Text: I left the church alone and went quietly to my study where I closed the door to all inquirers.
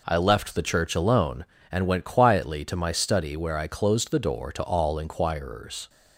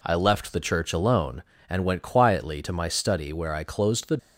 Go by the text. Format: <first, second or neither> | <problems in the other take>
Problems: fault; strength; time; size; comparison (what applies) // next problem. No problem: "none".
first | stops before "door to all inquirers"; at 4.1 s